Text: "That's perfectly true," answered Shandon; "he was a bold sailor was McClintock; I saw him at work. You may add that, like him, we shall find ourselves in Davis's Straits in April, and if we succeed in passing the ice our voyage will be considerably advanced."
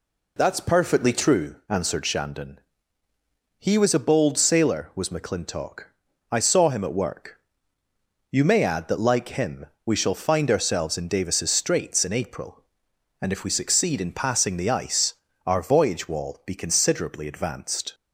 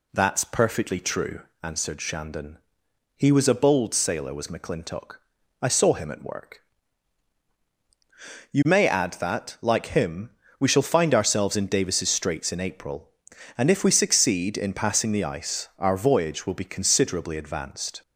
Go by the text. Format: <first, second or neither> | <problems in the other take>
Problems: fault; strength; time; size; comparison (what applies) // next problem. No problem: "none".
second | pauses between "ice" and "our"; slight; at 15.1 s; 0.32 s long // says "wall" for "will"; at 16.0 s